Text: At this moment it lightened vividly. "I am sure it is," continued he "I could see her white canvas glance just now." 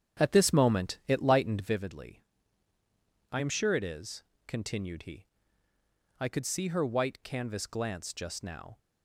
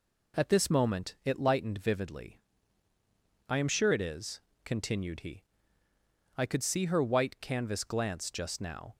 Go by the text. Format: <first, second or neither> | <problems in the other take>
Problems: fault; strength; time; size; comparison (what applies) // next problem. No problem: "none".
second | starts louder than the rest; strong; until 1.7 s; 8.5 dB // pauses between "he" and "I"; noticeable; at 5.2 s; 0.92 s long; noticeable in the second